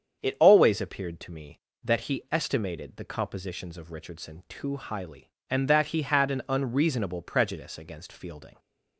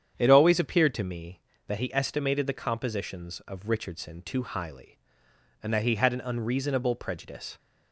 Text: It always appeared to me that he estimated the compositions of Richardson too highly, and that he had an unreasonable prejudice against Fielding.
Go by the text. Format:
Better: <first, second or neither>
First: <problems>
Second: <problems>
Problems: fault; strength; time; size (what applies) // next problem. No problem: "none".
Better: first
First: starts louder than the rest; strong; until 1.2 s; 7.5 dB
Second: starts louder than the rest; strong; until 1.1 s; 8.5 dB // stops before "against Fielding"; at 7.5 s